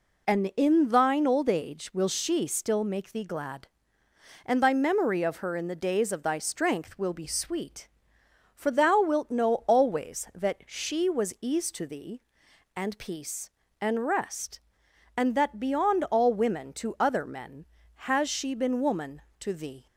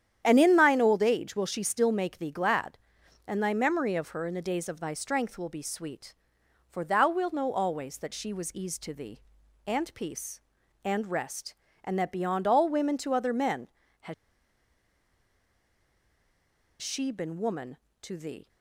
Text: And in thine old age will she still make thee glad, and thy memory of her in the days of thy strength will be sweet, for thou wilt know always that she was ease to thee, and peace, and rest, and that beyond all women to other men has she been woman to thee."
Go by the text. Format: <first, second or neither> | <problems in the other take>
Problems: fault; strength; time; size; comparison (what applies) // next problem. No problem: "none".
first | starts louder than the rest; strong; until 1.2 s; 9.5 dB // pauses between "has" and "she"; strong; at 14.1 s; 2.6 s long